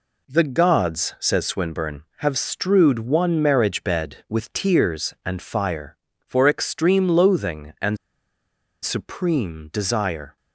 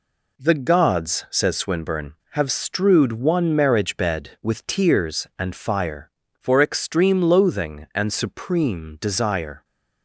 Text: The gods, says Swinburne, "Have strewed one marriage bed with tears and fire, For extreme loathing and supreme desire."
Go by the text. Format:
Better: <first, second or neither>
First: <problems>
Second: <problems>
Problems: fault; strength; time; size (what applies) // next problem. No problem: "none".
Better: second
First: pauses between "and" and "supreme"; noticeable; at 7.9 s; 0.87 s long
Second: none